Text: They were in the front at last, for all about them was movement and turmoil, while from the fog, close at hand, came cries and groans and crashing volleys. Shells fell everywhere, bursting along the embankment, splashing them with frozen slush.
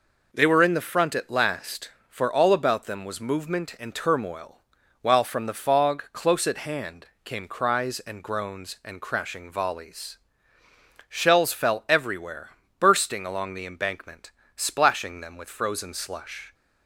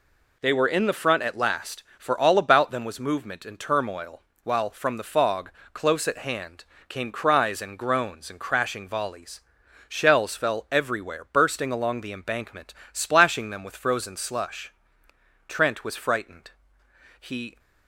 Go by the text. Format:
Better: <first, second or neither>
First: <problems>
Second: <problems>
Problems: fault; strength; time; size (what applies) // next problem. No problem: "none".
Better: first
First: none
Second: goes on to say "Trent was frightened He"; strong; from 15.4 s on; 2.1 s long